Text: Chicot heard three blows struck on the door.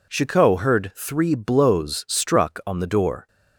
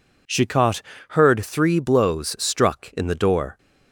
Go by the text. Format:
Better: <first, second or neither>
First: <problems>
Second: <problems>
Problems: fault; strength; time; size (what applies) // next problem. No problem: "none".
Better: first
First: none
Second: pauses between "Chicot" and "heard"; slight; at 0.8 s; 0.28 s long // says "in" for "on"; at 2.9 s